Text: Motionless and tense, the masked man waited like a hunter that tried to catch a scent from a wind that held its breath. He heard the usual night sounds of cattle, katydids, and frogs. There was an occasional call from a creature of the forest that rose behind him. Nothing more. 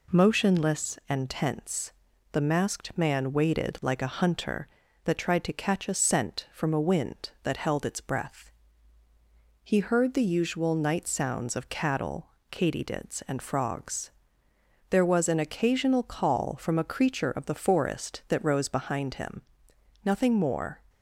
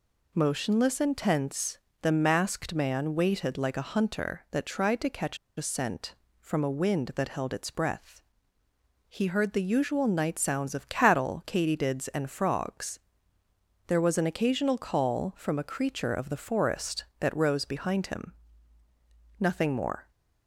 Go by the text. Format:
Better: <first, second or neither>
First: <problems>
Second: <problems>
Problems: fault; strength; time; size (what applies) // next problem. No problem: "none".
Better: first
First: none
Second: pauses between "catch" and "a"; slight; at 5.3 s; 0.20 s long